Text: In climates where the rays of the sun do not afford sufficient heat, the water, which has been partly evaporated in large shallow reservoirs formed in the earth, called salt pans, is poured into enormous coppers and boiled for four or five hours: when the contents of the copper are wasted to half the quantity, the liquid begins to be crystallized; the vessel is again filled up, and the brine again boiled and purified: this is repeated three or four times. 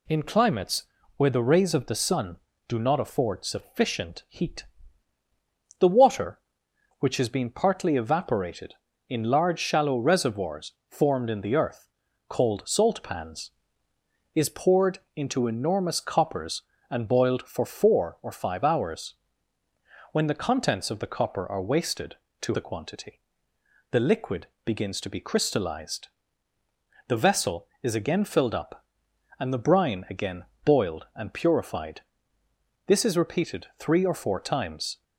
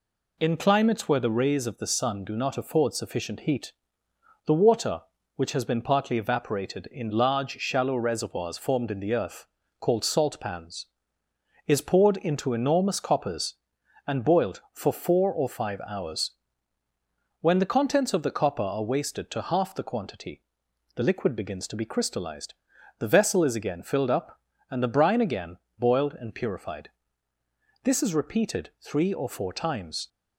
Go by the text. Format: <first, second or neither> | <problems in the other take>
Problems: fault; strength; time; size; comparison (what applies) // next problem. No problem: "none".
second | pauses between "climates" and "where"; slight; at 0.8 s; 0.32 s long // pauses between "reservoirs" and "formed"; slight; at 10.7 s; 0.16 s long // pauses between "poured" and "into"; slight; at 14.9 s; 0.16 s long // skips "half"; at 22.5 s // pauses between "liquid" and "begins"; slight; at 24.4 s; 0.18 s long // pauses between "again" and "boiled"; slight; at 30.4 s; 0.20 s long; slight in the second